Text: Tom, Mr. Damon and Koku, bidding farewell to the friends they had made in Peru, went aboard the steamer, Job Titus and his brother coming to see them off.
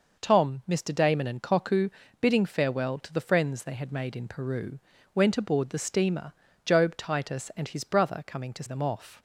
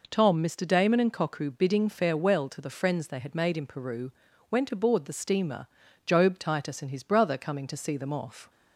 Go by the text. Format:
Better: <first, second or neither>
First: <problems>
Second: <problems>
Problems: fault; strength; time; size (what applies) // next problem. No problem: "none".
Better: second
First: skips "see"; at 8.6 s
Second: none